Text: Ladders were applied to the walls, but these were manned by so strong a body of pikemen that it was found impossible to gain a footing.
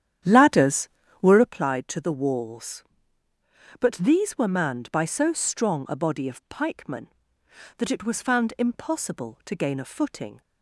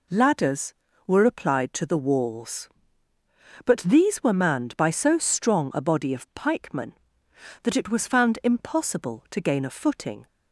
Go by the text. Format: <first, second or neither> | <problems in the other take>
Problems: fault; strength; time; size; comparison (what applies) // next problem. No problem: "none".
second | starts louder than the rest; strong; until 1.6 s; 10 dB